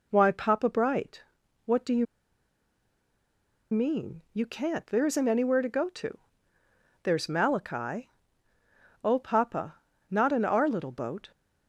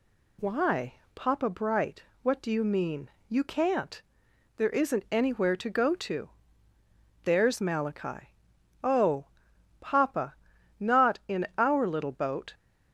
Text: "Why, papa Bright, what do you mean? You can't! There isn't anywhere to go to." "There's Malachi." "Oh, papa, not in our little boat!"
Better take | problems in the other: second | pauses between "you" and "mean"; strong; at 2.0 s; 1.6 s long

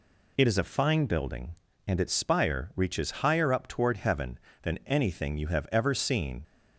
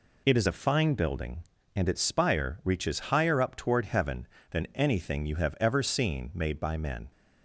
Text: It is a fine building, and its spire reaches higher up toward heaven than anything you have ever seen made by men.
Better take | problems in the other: second | stops before "made by men"; at 6.4 s

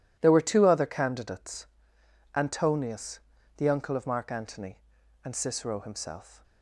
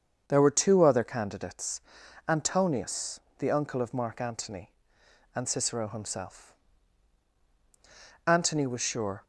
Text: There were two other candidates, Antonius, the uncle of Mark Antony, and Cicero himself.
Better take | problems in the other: first | starts louder than the rest; until 1.2 s; 7 dB // goes on to say "Antony was sure"; noticeable; from 8.2 s on; 0.98 s long

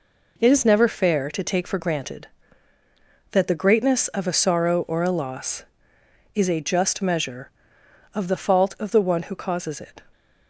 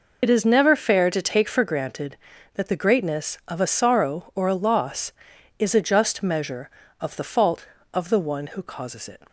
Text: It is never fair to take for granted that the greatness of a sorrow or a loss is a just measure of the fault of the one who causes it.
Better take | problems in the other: first | loses the start of "It"; at 0.2 s; 40 ms

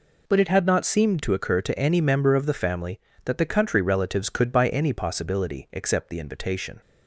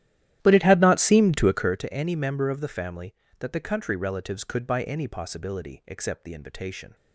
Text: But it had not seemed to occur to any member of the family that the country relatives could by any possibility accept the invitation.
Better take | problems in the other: first | starts louder than the rest; strong; until 1.8 s; 12.5 dB

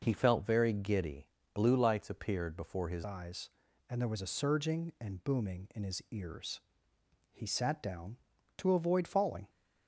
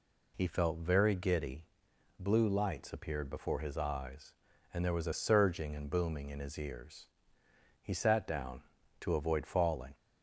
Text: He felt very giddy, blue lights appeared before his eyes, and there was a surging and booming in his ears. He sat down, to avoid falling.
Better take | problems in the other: second | changes voice at "eyes"; from 3.0 s on; 6.4 s long

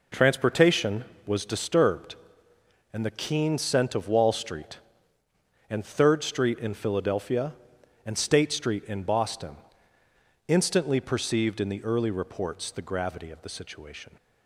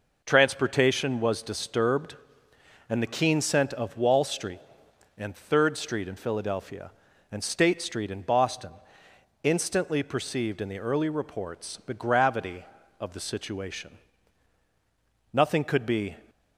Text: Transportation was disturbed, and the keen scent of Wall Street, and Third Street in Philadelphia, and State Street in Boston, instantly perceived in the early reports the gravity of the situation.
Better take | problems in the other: first | goes on to say "Nothing could be"; noticeable; from 15.3 s on; 0.84 s long

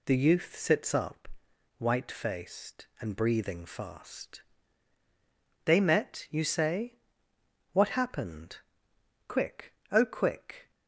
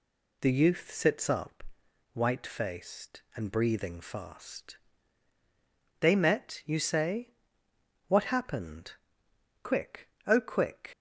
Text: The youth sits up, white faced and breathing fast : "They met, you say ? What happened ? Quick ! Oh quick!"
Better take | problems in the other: first | leaves "quick" unfinished; at 10.9 s; 120 ms

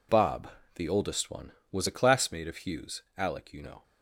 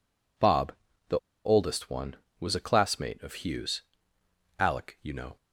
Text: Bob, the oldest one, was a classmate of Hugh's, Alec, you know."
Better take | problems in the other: first | pauses between "the" and "oldest"; slight; at 1.1 s; 0.28 s long

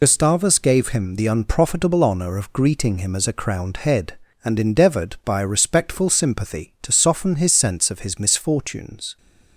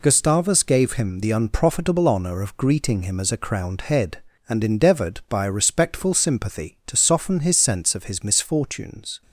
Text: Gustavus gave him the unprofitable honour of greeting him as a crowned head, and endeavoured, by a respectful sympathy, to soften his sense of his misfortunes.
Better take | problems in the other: second | loses the start of "Gustavus"; at 0.0 s; 60 ms

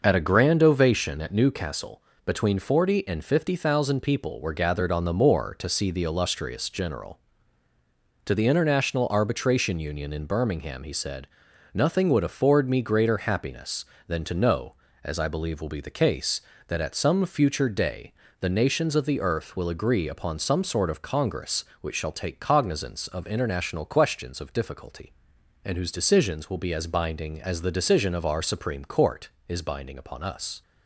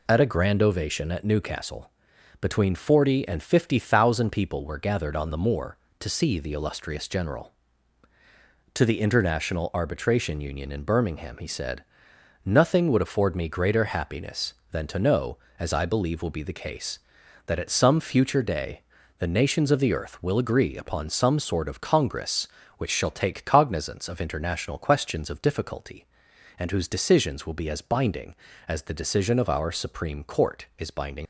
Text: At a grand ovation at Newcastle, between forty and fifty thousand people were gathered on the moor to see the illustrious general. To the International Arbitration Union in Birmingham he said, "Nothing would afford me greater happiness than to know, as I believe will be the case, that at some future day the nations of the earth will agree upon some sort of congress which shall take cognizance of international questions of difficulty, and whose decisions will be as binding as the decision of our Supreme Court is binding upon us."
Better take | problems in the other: first | pauses between "day" and "the"; slight; at 18.8 s; 0.36 s long; slight in the first // stops before "upon us"; at 31.2 s

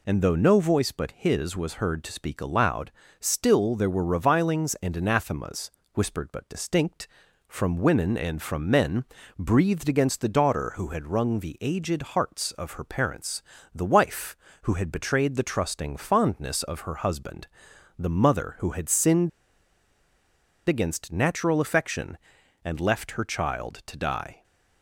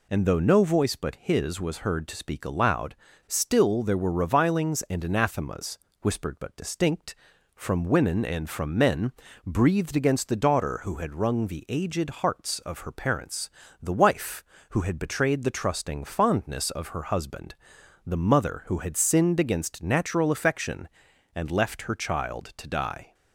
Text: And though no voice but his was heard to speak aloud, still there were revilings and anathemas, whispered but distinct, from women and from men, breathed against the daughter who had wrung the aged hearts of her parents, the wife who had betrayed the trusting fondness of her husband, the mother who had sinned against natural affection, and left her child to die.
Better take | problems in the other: second | pauses between "sinned" and "against"; strong; at 19.2 s; 1.3 s long

